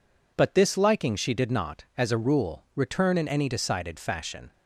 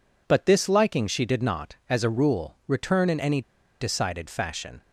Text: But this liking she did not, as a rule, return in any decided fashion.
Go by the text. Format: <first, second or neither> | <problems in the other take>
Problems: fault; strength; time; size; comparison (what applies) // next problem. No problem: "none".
first | pauses between "any" and "decided"; at 3.4 s; 0.39 s long